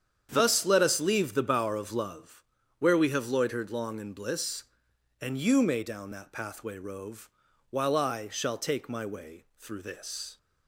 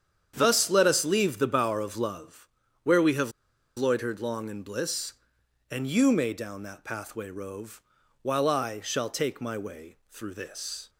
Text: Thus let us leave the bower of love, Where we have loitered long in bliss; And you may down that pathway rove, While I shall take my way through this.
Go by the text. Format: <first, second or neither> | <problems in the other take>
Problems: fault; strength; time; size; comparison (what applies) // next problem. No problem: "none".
first | starts louder than the rest; strong; until 1.3 s; 8.5 dB; strong in the first // pauses between "have" and "loitered"; at 3.3 s; 0.45 s long